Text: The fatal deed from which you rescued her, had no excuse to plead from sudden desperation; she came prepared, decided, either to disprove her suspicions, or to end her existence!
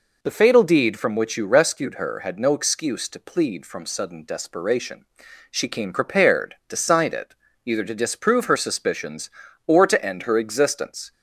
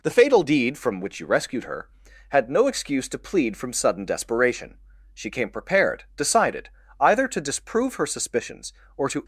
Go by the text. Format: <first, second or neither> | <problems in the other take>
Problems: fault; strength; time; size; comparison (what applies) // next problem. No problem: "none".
first | stops before "end her existence"; at 9.2 s